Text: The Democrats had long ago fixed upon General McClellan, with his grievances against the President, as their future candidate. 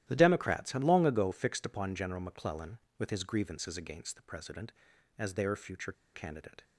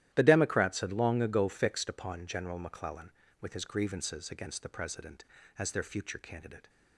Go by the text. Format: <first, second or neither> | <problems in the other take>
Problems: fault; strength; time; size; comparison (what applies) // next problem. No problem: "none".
second | starts louder than the rest; strong; until 1.0 s; 12.5 dB; strong in the second // pauses between "future" and "candidate"; slight; at 5.9 s; 0.22 s long